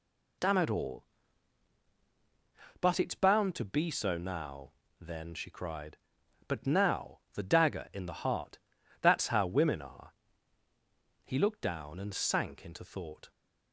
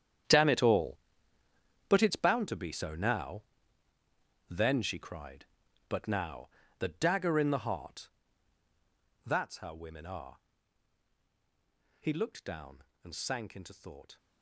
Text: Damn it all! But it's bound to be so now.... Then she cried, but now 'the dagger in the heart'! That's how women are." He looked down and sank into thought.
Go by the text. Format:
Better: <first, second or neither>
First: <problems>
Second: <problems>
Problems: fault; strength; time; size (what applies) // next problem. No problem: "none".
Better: first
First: pauses between "now" and "the"; slight; at 7.1 s; 0.16 s long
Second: gets quieter; strong; throughout; 14 dB // pauses between "now" and "the"; slight; at 6.4 s; 0.30 s long